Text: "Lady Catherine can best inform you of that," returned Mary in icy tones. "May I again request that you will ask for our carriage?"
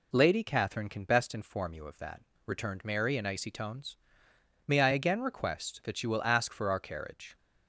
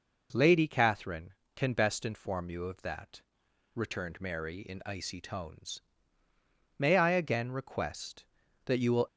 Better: first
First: none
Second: stops before "ask for our carriage"; at 9.0 s

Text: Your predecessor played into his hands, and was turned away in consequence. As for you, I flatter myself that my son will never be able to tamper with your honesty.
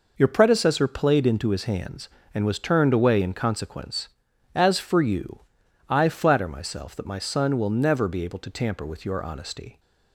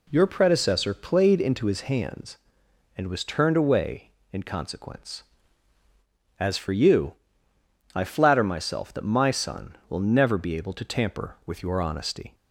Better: neither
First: none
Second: none

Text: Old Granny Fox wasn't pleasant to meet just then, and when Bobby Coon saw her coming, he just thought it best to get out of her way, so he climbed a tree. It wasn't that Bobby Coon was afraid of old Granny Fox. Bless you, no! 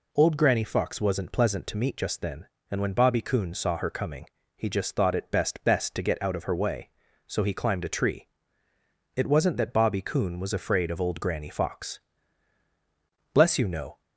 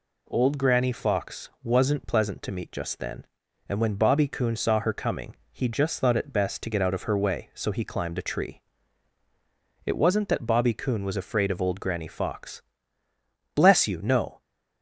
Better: second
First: says "best" twice; at 5.6 s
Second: none

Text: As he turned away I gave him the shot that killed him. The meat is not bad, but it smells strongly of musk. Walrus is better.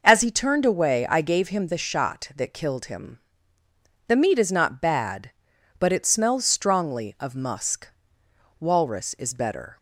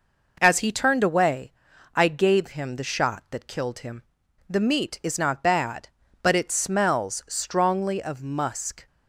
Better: first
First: none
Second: pauses between "away" and "I"; noticeable; at 1.5 s; 0.46 s long // stops before "Walrus is better"; at 8.8 s

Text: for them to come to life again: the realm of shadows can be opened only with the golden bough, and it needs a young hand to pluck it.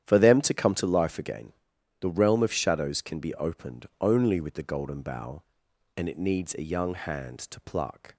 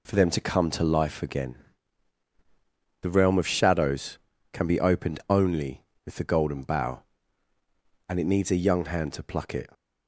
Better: second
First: starts louder than the rest; strong; until 1.0 s; 10.5 dB // pauses between "opened" and "only"; slight; at 3.8 s; 0.16 s long // stops before "it"; at 8.1 s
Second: none

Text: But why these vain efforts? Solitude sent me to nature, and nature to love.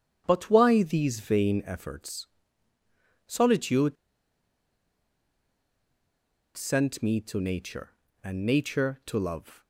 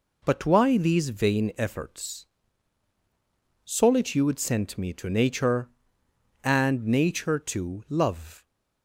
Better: second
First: starts louder than the rest; strong; until 1.2 s; 9 dB // pauses between "Solitude" and "sent"; strong; at 3.9 s; 2.6 s long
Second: none

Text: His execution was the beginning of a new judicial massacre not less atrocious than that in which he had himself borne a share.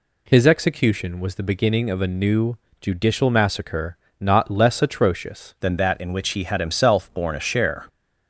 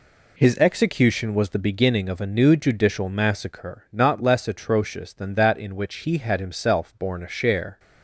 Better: second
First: pauses between "new" and "judicial"; slight; at 2.5 s; 0.24 s long // pauses between "massacre" and "not"; slight; at 3.9 s; 0.24 s long // changes voice at "than"; from 5.6 s on; 2.2 s long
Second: none

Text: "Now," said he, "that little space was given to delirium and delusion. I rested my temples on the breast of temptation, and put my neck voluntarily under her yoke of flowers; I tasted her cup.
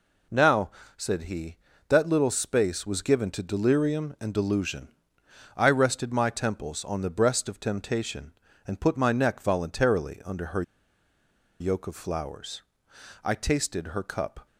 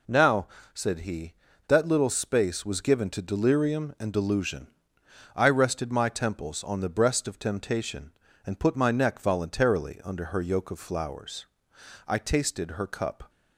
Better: second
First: pauses between "her" and "yoke"; noticeable; at 10.6 s; 0.98 s long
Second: none

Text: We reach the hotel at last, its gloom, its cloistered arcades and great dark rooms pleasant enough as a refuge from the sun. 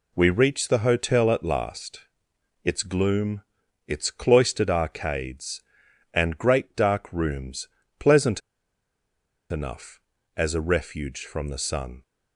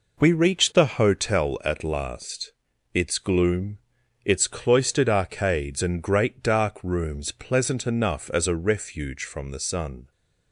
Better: second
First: pauses between "rooms" and "pleasant"; slight; at 7.6 s; 0.32 s long // pauses between "pleasant" and "enough"; at 8.4 s; 1.1 s long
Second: none

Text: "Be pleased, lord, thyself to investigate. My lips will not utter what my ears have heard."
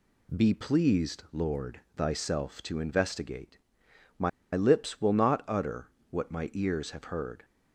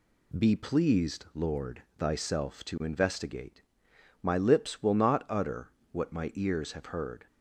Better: second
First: pauses between "My" and "lips"; slight; at 4.2 s; 0.24 s long // pauses between "utter" and "what"; slight; at 5.8 s; 0.24 s long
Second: pauses between "utter" and "what"; slight; at 5.6 s; 0.24 s long

